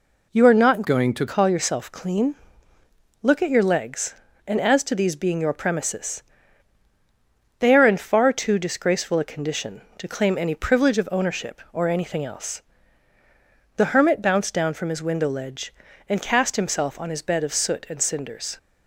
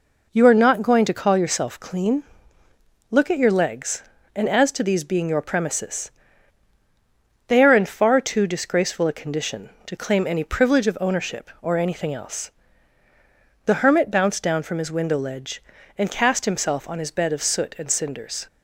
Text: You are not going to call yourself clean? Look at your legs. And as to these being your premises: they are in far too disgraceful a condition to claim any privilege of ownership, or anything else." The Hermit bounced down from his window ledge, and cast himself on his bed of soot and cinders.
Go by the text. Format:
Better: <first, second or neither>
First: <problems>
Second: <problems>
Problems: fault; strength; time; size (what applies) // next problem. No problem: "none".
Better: second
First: changes voice from "going" to "to"; from 0.8 to 1.2 s; 0.4 s long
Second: none